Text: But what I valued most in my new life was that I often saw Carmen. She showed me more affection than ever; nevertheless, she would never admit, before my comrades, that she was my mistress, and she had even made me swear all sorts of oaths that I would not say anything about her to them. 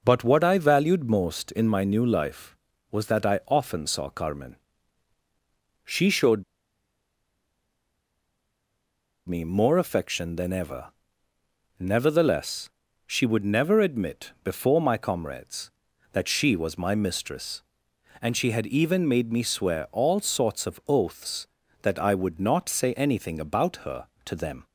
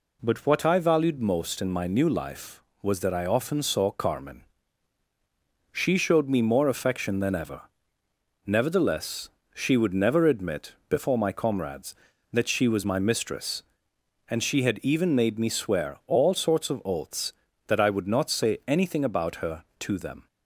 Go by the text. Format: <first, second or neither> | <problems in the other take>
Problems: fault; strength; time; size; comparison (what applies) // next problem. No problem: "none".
second | pauses between "showed" and "me"; strong; at 6.4 s; 2.8 s long